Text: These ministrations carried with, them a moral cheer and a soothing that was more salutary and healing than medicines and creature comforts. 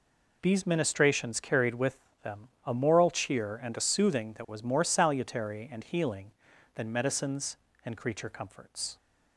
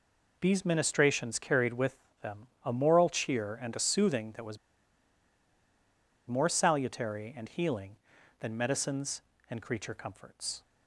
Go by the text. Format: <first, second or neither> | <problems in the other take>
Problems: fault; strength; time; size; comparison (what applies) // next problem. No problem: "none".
first | pauses between "them" and "a"; slight; at 2.4 s; 0.16 s long; slight in the first // pauses between "was" and "more"; strong; at 4.5 s; 1.6 s long